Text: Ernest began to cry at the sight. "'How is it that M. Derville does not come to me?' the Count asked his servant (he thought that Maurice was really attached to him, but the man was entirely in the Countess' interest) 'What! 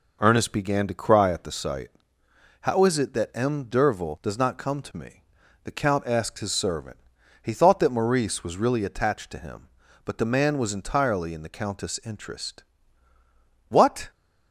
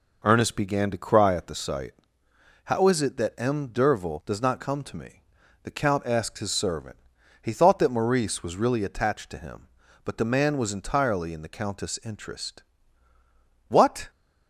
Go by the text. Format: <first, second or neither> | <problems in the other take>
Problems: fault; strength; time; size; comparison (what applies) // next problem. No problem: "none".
neither | none